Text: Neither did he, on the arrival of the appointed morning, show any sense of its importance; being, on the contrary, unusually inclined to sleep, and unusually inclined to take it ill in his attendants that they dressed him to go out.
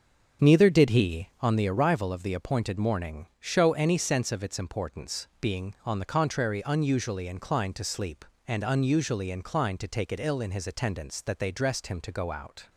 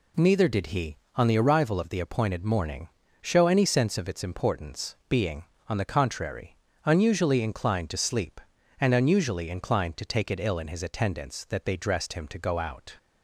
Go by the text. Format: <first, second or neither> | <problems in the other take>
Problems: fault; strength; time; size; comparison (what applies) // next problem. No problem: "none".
second | starts louder than the rest; strong; until 1.6 s; 7 dB